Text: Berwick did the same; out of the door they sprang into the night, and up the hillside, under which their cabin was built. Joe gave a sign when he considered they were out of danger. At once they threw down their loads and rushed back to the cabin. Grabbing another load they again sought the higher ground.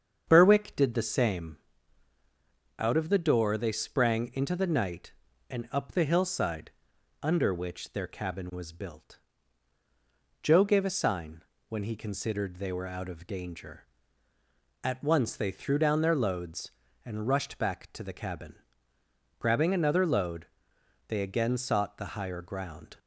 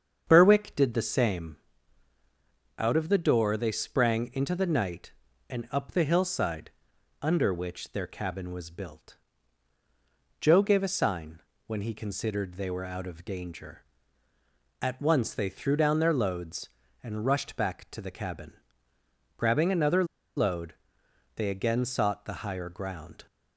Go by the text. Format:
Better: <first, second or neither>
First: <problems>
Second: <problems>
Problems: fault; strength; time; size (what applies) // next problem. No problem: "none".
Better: first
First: starts louder than the rest; strong; until 1.2 s; 7.5 dB // pauses between "sign" and "when"; slight; at 11.4 s; 0.26 s long // pauses between "load" and "they"; noticeable; at 20.4 s; 0.62 s long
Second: starts louder than the rest; strong; until 1.2 s; 7.5 dB // pauses between "sign" and "when"; slight; at 11.4 s; 0.26 s long // pauses between "another" and "load"; slight; at 20.0 s; 0.32 s long // pauses between "load" and "they"; noticeable; at 20.7 s; 0.62 s long